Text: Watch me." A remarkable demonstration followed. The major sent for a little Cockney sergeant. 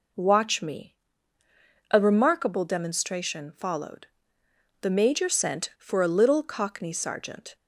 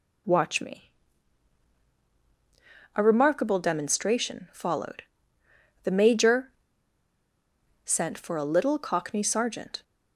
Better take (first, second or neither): first